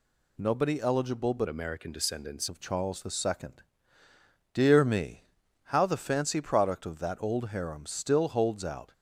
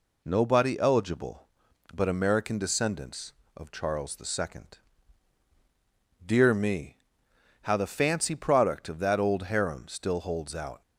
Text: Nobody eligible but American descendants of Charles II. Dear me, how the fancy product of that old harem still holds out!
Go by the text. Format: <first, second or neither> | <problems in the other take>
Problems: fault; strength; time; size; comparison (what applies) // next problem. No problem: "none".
second | changes voice from "American" to "descendants"; from 1.4 to 2.4 s; 1.0 s long